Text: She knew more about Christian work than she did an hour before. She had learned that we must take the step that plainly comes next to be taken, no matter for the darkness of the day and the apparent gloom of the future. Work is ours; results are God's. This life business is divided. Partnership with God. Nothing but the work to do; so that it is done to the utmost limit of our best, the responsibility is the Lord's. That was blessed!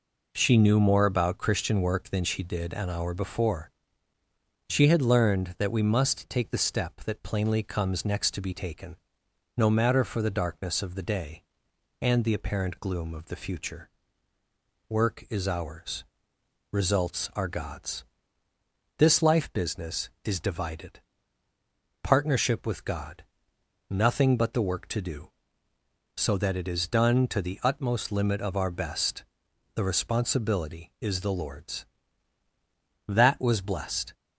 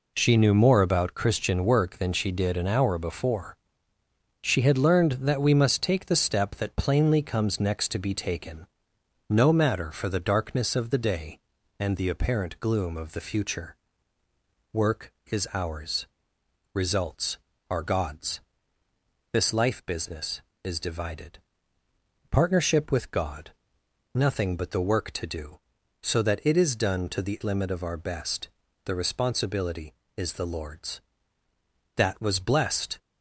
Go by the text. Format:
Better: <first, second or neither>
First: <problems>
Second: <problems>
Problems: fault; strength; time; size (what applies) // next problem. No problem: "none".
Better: first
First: none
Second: skips "utmost"; at 27.4 s